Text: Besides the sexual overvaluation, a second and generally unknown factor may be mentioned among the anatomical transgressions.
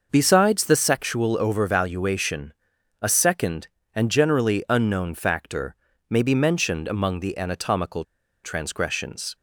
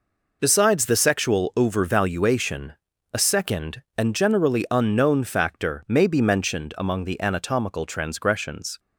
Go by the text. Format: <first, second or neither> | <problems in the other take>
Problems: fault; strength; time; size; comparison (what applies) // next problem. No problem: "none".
second | pauses between "factor" and "may"; slight; at 5.7 s; 0.32 s long // pauses between "anatomical" and "transgressions"; at 8.0 s; 0.41 s long